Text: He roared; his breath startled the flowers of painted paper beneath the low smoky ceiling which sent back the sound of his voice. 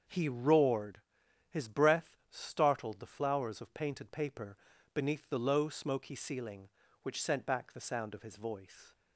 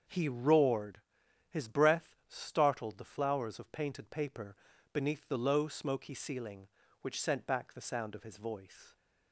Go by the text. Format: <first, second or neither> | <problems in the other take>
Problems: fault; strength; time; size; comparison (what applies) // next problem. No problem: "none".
neither | starts louder than the rest; the same in both // pauses between "paper" and "beneath"; the same in both